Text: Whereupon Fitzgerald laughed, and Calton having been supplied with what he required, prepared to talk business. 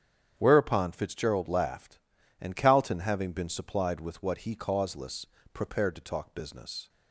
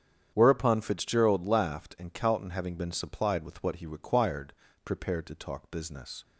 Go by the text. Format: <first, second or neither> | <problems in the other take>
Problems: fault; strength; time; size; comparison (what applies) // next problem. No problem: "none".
second | starts louder than the rest; strong; until 1.3 s; 8.5 dB; strong in the second // says "causeless" for "required"; at 4.5 s